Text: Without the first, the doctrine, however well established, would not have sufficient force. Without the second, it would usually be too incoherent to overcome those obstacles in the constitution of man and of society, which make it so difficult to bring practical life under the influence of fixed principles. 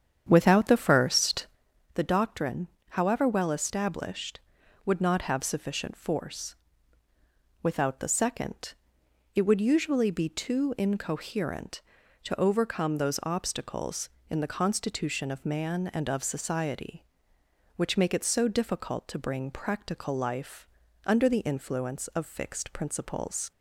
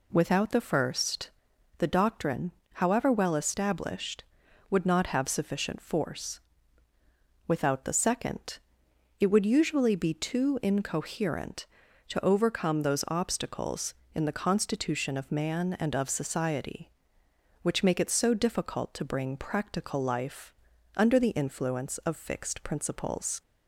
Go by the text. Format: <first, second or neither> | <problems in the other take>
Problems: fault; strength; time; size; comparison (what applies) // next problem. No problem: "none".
second | starts louder than the rest; strong; until 1.6 s; 8.5 dB // pauses between "life" and "under"; at 20.6 s; 0.38 s long; also in the second